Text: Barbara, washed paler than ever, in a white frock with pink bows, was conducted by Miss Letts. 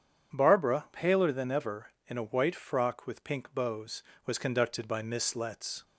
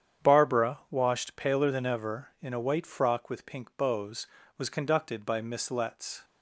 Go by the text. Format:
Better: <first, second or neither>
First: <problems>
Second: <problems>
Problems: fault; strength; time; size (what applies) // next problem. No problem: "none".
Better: second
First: starts louder than the rest; strong; until 1.4 s; 8 dB // skips "washed"; at 0.8 s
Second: starts louder than the rest; strong; until 1.3 s; 8.5 dB